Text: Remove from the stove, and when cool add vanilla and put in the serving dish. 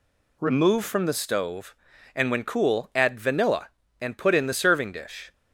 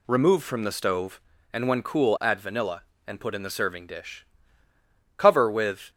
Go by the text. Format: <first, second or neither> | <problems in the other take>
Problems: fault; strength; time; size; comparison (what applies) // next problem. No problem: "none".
first | goes on to say "Cover with"; noticeable; from 5.1 s on; 0.74 s long